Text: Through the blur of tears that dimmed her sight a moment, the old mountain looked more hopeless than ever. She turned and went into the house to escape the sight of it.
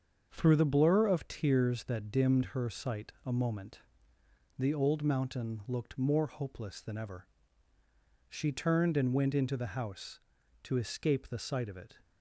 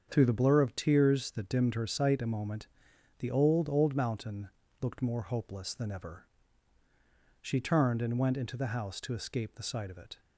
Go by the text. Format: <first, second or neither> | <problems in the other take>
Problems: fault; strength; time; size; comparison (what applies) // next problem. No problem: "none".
first | starts louder than the rest; strong; until 1.1 s; 7 dB; also in the first // says "old" twice; at 3.6 s // pauses between "mountain" and "looked"; slight; at 4.4 s; 0.32 s long